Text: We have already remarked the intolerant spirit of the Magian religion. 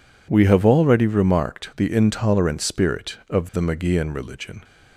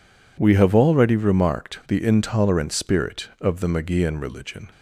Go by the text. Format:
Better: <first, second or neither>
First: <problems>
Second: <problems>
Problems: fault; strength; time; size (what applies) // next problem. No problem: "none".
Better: neither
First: none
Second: none